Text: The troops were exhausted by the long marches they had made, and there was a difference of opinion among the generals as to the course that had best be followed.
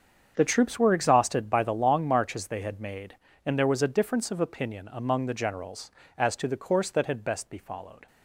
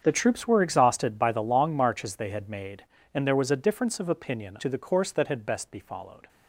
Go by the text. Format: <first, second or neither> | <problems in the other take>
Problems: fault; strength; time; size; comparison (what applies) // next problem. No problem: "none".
first | starts louder than the rest; strong; until 1.0 s; 7.5 dB; strong in the first // skips "among the generals as"; at 4.5 s